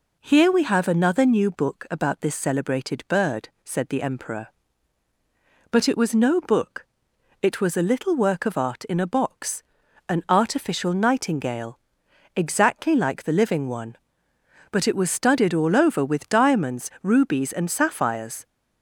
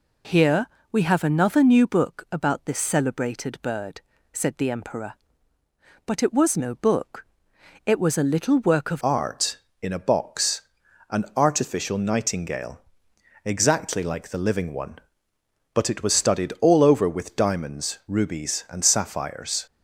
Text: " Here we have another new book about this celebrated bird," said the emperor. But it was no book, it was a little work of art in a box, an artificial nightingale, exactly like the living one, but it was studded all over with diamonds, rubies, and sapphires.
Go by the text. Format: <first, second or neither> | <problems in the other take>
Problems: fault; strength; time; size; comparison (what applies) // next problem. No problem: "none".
first | pauses between "Here" and "we"; slight; at 0.6 s; 0.24 s long // changes voice at "art"; from 9.0 s on; 10.6 s long